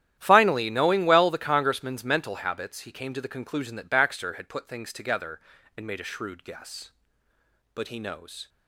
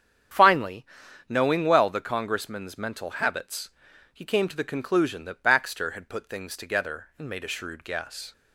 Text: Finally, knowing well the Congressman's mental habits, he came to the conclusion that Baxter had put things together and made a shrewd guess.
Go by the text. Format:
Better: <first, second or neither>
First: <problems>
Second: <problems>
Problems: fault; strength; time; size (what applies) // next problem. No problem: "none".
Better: second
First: starts louder than the rest; strong; until 1.1 s; 11.5 dB // goes on to say "But he knows"; noticeable; from 7.7 s on; 0.76 s long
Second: starts louder than the rest; strong; until 1.7 s; 8.5 dB